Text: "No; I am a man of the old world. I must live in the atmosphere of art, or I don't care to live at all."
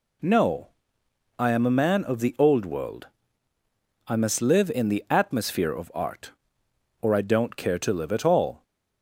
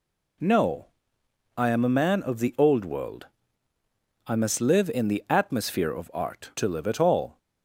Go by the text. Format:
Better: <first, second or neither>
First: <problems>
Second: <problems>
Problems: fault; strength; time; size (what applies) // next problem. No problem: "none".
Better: first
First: none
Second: skips "or I don't care"; at 6.5 s